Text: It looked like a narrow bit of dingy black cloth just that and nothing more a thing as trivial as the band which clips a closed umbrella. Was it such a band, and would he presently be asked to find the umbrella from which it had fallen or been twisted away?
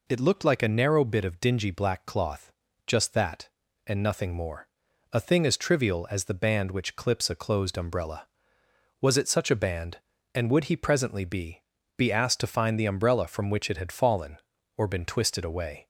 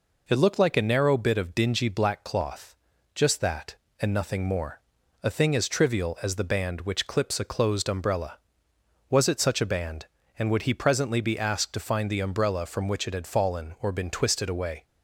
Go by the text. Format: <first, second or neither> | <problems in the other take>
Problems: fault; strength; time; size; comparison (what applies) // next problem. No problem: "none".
second | pauses between "cloth" and "just"; slight; at 2.5 s; 0.34 s long; also in the second // pauses between "more" and "a"; at 4.6 s; 0.42 s long; also in the second // says "be" twice; at 11.9 s